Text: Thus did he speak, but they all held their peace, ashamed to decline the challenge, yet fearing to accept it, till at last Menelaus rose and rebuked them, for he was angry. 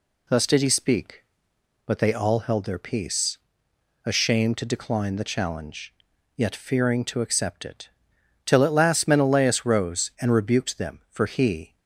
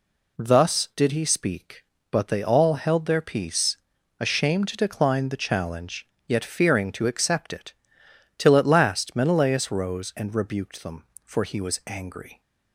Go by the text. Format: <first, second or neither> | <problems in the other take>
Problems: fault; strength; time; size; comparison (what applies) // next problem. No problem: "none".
second | stops before "was angry"; at 11.7 s